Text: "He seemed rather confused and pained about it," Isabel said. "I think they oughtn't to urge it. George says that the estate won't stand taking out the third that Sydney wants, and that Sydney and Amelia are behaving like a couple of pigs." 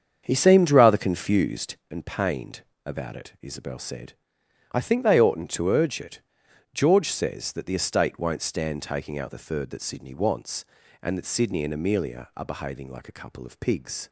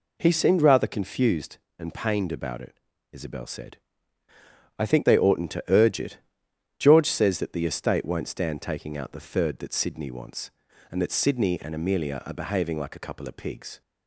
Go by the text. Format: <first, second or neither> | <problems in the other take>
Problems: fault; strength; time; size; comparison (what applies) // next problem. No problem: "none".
second | starts louder than the rest; strong; until 1.8 s; 7.5 dB // pauses between "pained" and "about"; slight; at 2.6 s; 0.24 s long